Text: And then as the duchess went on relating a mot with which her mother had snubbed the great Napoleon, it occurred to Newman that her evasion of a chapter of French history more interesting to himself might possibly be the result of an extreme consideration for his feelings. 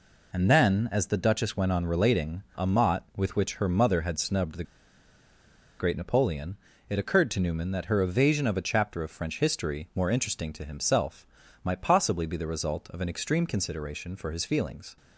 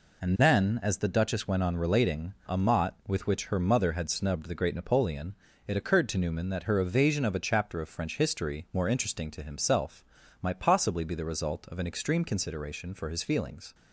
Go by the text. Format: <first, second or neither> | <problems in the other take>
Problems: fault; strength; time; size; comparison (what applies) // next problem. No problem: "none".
second | pauses between "the" and "great"; at 4.6 s; 1.1 s long // pauses between "himself" and "might"; slight; at 11.2 s; 0.36 s long; slight in the second